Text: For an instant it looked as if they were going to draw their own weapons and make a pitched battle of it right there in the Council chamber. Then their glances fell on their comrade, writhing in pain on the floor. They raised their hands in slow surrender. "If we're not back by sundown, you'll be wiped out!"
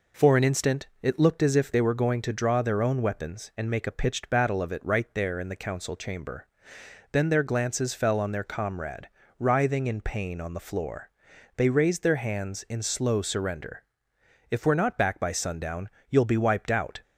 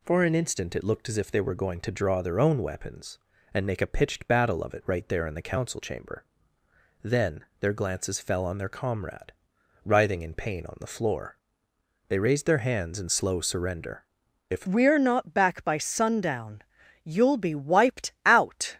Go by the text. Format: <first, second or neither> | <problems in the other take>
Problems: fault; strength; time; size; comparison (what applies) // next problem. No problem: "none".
first | pauses between "Then" and "their"; slight; at 7.4 s; 0.16 s long // changes voice at "we're"; from 14.6 s on; 4.1 s long